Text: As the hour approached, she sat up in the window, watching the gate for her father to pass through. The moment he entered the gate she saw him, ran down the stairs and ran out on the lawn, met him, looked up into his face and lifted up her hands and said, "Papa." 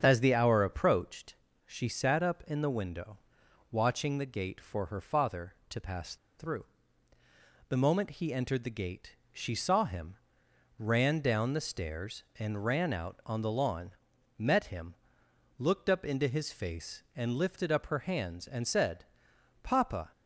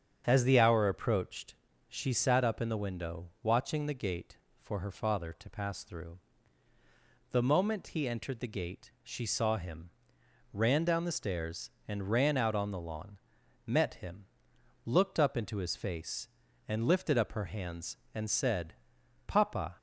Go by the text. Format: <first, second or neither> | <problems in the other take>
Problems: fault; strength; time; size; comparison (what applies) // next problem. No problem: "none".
second | starts louder than the rest; strong; until 1.0 s; 7.5 dB; strong in the second // pauses between "pass" and "through"; slight; at 6.1 s; 0.23 s long // pauses between "gate" and "she"; slight; at 9.1 s; 0.18 s long